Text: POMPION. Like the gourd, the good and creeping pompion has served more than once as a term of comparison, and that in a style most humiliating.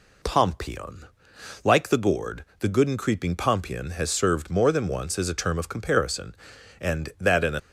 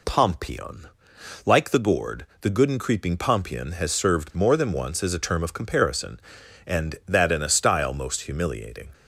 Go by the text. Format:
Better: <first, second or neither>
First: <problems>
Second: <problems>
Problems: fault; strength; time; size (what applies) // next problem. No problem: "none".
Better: second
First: stops before "style most humiliating"; at 7.5 s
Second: none